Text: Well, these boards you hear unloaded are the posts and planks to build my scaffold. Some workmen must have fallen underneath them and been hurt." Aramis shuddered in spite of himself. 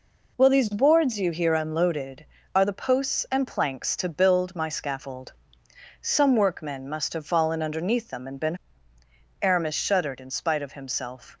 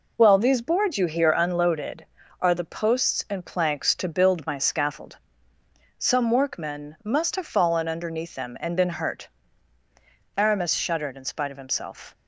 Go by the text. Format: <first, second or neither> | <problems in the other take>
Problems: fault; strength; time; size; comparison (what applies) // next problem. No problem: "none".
second | skips "hurt"; at 8.9 s